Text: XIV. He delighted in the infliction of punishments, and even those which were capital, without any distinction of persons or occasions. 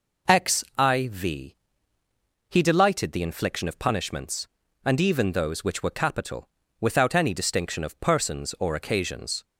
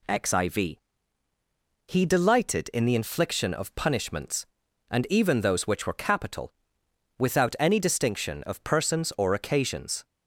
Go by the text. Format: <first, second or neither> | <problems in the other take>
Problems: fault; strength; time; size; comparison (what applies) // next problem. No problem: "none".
second | skips "in"; at 3.1 s